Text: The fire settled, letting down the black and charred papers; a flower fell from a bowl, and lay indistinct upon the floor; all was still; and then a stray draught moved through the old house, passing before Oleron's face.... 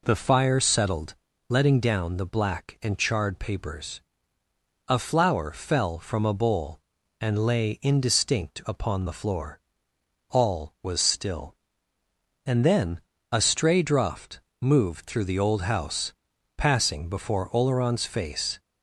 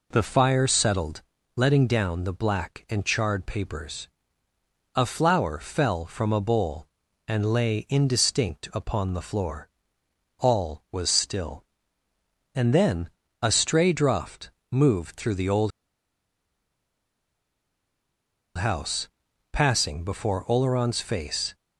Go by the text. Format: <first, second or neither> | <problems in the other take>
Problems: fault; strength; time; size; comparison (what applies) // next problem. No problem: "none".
first | pauses between "then" and "a"; slight; at 13.0 s; 0.34 s long; slight in the first // pauses between "draught" and "moved"; slight; at 14.5 s; 0.18 s long; slight in the first // pauses between "old" and "house"; strong; at 15.7 s; 2.8 s long